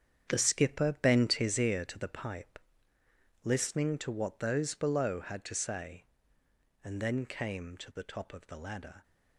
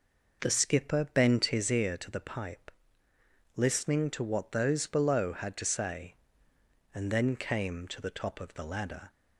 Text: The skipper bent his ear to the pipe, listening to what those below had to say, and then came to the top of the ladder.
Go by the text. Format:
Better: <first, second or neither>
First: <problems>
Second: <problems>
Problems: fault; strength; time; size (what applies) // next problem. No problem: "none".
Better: second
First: gets quieter; strong; throughout; 10 dB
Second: none